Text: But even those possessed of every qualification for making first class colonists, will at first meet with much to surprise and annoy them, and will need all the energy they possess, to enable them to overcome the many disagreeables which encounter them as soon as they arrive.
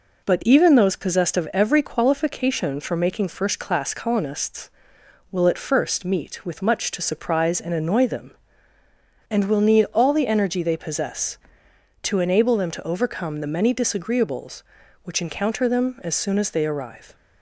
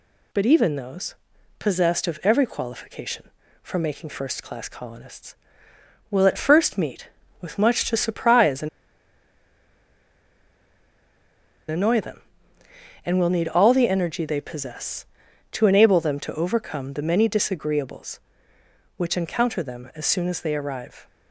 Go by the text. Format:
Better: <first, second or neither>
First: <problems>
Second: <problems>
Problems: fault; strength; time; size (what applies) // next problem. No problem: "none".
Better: first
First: none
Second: pauses between "those" and "possessed"; at 1.1 s; 0.44 s long // pauses between "and" and "annoy"; strong; at 8.6 s; 3.0 s long